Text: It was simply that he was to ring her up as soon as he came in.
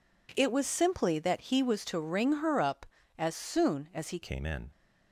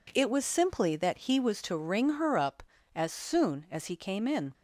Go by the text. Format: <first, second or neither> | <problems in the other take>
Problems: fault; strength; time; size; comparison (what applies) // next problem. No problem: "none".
second | changes voice at "came"; from 4.2 s on; 0.4 s long